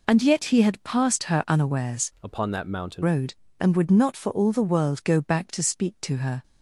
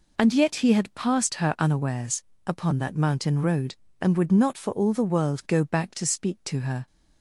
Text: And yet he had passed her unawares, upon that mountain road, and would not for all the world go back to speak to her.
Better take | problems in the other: second | changes voice from "upon" to "mountain"; from 2.2 to 3.0 s; 0.8 s long

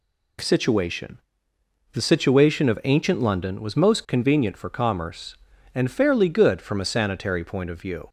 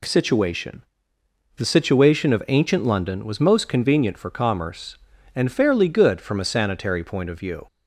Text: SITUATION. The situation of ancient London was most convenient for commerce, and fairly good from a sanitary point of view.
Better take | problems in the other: neither | none

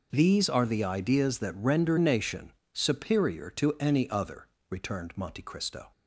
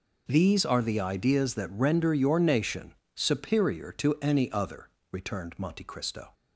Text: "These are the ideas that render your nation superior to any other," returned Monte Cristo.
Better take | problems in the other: second | skips "your"; at 1.9 s // pauses between "nation" and "superior"; slight; at 2.5 s; 0.22 s long; slight in the second

